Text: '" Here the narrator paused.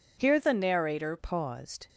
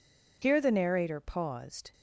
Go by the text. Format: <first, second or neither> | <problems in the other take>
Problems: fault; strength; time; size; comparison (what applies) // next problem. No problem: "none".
second | changes voice from "the" to "narrator"; from 0.3 to 1.1 s; 0.8 s long